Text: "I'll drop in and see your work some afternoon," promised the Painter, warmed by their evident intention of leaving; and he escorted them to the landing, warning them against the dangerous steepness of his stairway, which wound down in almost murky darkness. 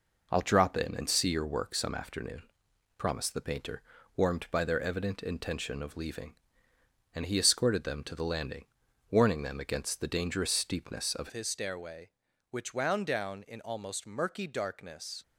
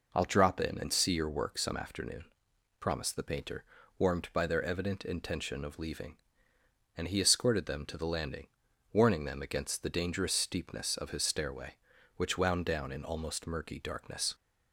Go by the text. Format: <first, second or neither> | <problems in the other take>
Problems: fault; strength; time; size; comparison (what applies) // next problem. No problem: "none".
second | changes voice at "his"; from 11.3 s on; 3.9 s long